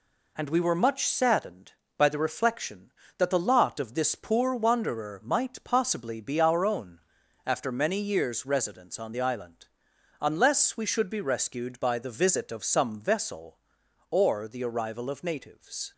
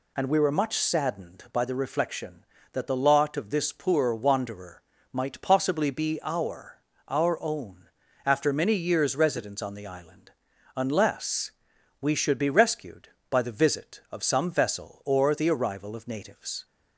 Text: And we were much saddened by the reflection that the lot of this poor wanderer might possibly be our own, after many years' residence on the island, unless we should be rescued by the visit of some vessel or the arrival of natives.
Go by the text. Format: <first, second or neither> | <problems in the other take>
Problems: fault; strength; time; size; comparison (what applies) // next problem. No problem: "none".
first | pauses between "wanderer" and "might"; slight; at 4.8 s; 0.30 s long // says "our" twice; at 7.0 s // pauses between "unless" and "we"; noticeable; at 11.4 s; 0.50 s long